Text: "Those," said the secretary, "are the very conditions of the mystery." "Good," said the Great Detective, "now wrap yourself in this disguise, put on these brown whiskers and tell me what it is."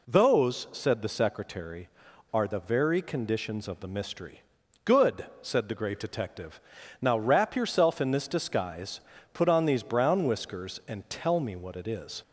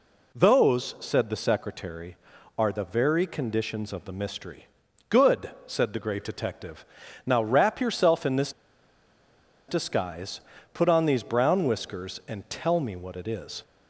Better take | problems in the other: first | pauses between "this" and "disguise"; at 8.5 s; 1.1 s long

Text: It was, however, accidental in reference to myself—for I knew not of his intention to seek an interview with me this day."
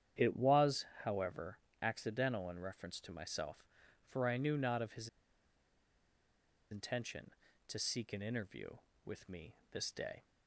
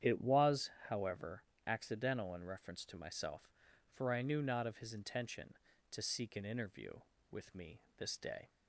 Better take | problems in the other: second | starts louder than the rest; strong; until 1.3 s; 9 dB; strong in the second // pauses between "his" and "intention"; strong; at 5.0 s; 1.6 s long // pauses between "me" and "this"; slight; at 9.5 s; 0.16 s long; slight in the second

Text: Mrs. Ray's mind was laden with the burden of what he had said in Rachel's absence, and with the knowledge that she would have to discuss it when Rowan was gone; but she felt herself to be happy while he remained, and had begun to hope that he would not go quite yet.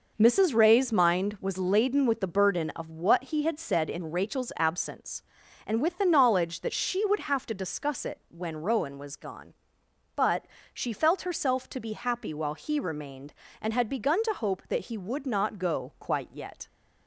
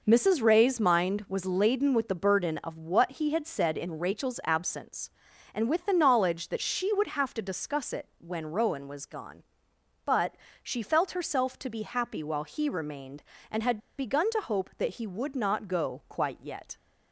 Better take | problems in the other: first | pauses between "but" and "she"; slight; at 10.3 s; 0.28 s long; slight in the first // pauses between "had" and "begun"; slight; at 13.7 s; 0.20 s long

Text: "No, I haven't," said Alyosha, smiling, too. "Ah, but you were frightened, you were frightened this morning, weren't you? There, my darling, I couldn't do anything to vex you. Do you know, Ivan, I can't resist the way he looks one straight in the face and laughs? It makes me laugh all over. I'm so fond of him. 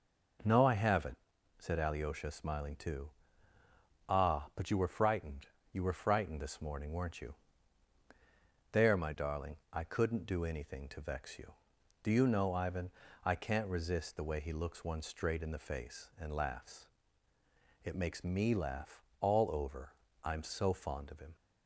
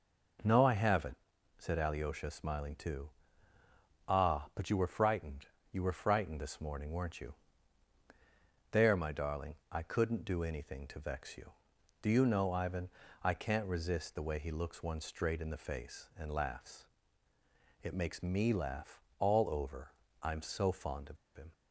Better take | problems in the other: first | pauses between "laugh" and "all"; slight; at 19.0 s; 0.16 s long; slight in the first // pauses between "of" and "him"; slight; at 21.1 s; 0.19 s long

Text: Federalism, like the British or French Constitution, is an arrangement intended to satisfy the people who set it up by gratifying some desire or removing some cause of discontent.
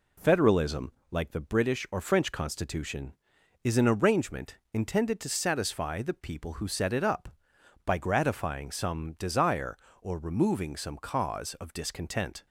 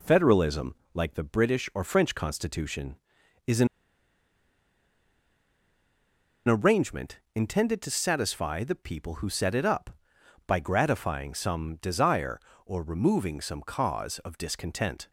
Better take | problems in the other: first | pauses between "an" and "arrangement"; strong; at 3.6 s; 2.8 s long

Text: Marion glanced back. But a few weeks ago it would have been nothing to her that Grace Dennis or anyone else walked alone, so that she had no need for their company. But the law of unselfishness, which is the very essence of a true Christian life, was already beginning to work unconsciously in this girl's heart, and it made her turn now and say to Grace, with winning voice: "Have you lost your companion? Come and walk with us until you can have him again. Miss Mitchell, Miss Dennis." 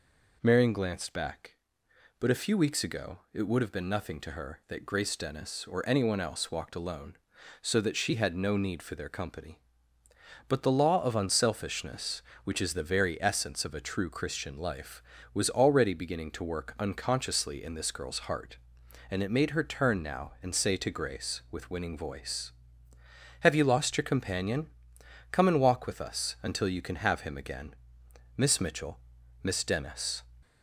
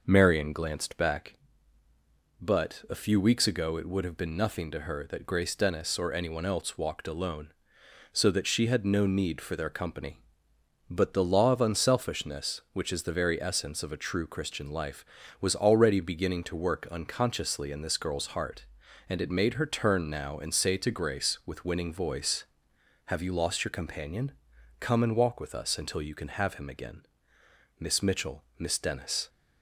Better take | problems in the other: neither | none

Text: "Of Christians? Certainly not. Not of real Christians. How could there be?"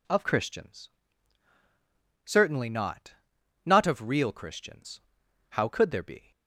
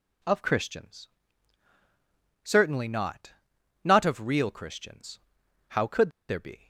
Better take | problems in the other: first | pauses between "could" and "there"; slight; at 6.0 s; 0.19 s long

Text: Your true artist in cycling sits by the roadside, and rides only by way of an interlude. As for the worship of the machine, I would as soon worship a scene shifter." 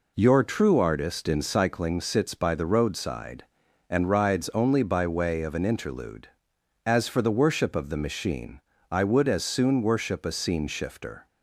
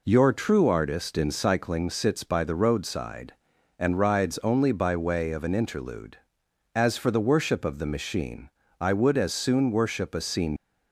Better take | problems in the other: first | stops before "shifter"; at 10.5 s

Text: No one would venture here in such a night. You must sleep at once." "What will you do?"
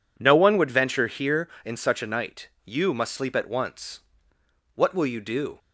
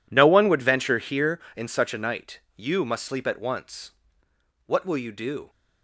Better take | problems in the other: first | gets quieter; strong; throughout; 15.5 dB

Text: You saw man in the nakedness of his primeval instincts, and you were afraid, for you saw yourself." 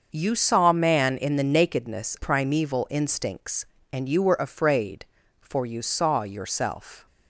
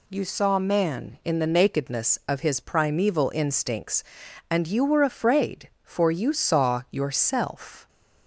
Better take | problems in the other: second | starts louder than the rest; until 1.1 s; 6.5 dB // skips "of his"; at 2.1 s

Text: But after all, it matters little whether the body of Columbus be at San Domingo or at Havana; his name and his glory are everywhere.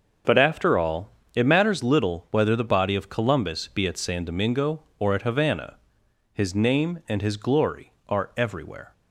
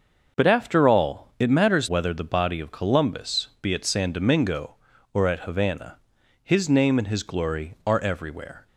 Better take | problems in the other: first | starts louder than the rest; noticeable; until 1.4 s; 6 dB; also in the first // skips "little"; at 1.8 s

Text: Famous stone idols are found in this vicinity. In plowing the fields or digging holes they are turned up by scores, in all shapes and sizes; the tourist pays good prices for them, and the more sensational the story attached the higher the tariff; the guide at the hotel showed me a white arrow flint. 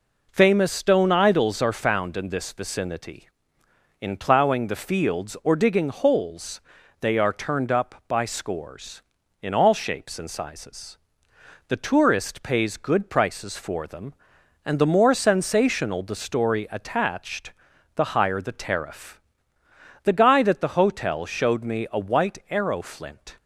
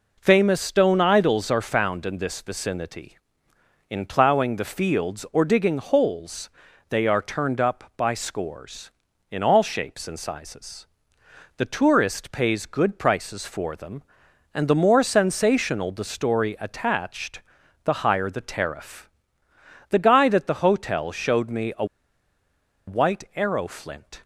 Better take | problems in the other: first | pauses between "holes" and "they"; at 6.4 s; 0.40 s long; also in the first // pauses between "attached" and "the"; at 17.4 s; 0.44 s long; also in the first // pauses between "a" and "white"; at 21.8 s; 1.0 s long

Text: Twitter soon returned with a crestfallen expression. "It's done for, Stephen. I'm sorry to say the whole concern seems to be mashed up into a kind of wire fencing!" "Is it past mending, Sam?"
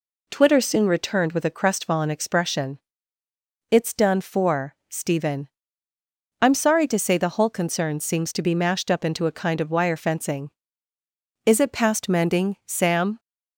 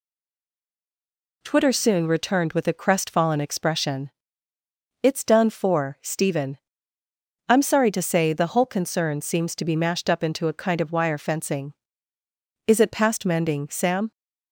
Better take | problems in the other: first | stays silent before the first word; noticeable; until 1.4 s; 1.4 s long

